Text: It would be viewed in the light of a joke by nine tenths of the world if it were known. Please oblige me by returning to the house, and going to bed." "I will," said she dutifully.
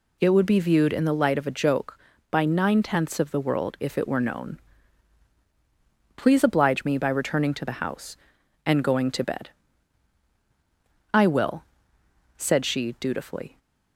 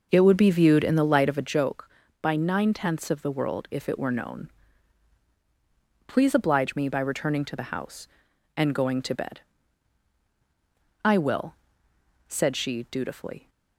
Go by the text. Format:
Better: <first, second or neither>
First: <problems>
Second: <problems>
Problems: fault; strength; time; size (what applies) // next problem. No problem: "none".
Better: first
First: none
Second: starts louder than the rest; noticeable; until 1.6 s; 5.5 dB